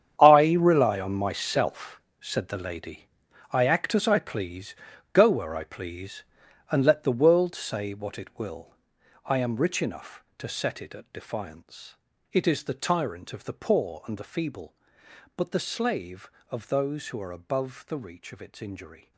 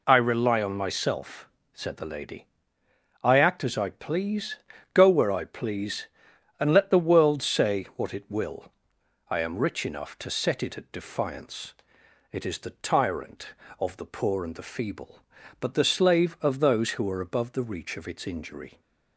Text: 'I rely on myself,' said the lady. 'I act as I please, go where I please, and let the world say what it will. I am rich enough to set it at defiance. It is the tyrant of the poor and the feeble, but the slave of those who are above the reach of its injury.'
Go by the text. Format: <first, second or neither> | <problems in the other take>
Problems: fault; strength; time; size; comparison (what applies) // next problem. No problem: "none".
second | gets quieter; strong; throughout; 14.5 dB